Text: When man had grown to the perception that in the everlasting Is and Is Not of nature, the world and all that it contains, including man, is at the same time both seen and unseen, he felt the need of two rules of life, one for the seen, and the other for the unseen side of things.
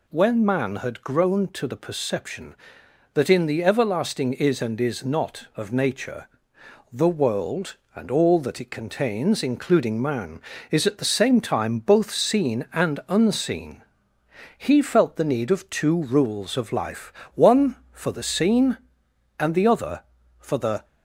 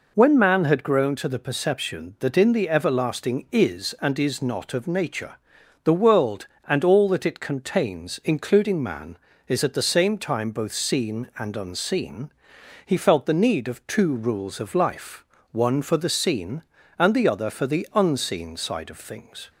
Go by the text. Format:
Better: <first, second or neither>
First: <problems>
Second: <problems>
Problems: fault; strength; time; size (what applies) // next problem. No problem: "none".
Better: second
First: stops before "unseen side of things"; at 20.8 s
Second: none